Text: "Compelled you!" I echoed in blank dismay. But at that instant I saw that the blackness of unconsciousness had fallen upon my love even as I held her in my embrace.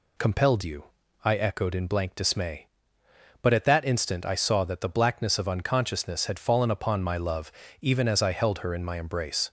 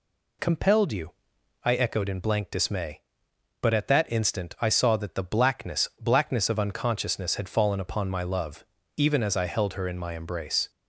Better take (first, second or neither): first